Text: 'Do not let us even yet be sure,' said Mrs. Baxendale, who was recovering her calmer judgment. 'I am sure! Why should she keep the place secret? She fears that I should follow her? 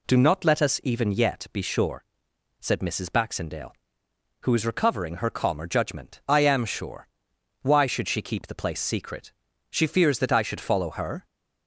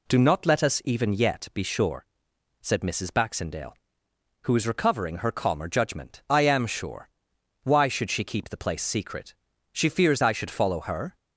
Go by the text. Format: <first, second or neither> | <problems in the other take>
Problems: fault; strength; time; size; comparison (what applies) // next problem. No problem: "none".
first | skips "that"; at 10.2 s